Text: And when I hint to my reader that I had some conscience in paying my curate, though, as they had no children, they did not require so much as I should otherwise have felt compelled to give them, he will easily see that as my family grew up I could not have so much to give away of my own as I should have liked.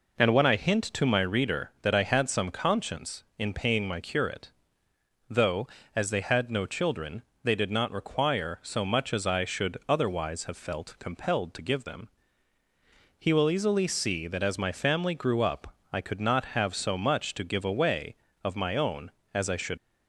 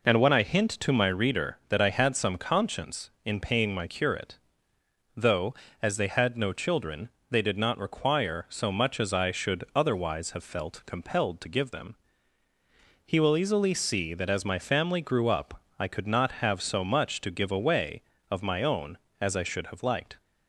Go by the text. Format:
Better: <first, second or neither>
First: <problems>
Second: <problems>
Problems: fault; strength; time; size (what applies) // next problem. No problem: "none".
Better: second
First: pauses between "up" and "I"; slight; at 15.7 s; 0.18 s long // stops before "have liked"; at 19.7 s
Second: pauses between "up" and "I"; slight; at 15.6 s; 0.18 s long